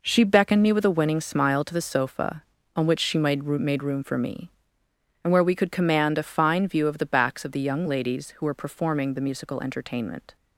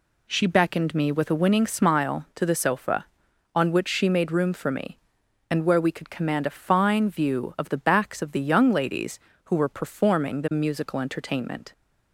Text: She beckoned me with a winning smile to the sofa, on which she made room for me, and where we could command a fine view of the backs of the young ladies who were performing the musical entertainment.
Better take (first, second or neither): second